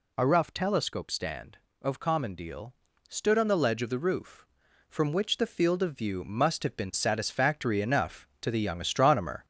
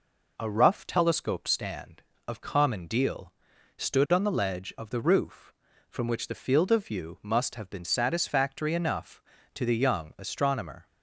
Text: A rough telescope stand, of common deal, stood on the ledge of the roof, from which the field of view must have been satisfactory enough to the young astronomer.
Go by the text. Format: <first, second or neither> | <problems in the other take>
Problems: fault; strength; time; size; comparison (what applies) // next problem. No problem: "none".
second | gets louder; throughout; 4 dB